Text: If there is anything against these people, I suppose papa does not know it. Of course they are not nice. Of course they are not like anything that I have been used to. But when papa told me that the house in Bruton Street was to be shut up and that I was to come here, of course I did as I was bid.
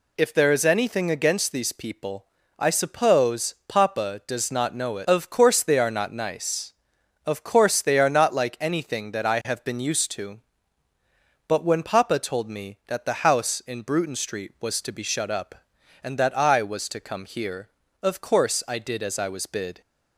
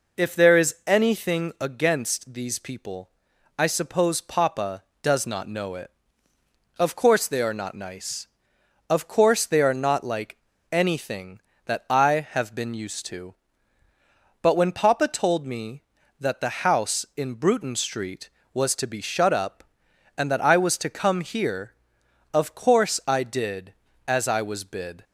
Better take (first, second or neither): first